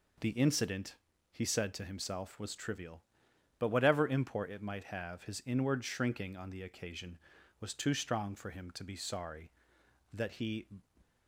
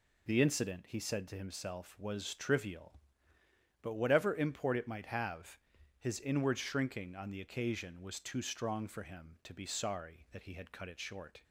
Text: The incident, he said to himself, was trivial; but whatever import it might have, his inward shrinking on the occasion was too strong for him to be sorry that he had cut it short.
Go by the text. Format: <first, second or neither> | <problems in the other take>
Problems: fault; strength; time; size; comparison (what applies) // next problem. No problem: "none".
second | stops before "had cut it short"; at 11.0 s